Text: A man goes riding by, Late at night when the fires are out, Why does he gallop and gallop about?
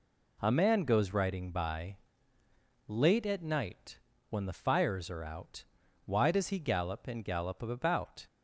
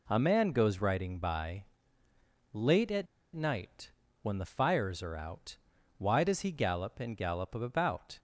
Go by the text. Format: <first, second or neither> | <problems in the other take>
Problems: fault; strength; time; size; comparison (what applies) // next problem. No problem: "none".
first | pauses between "at" and "night"; slight; at 3.0 s; 0.29 s long // pauses between "night" and "when"; slight; at 3.9 s; 0.32 s long; slight in the first